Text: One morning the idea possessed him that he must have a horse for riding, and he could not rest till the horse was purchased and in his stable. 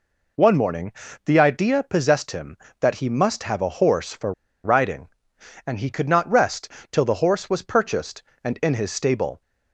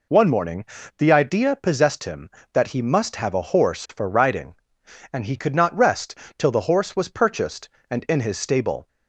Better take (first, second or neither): second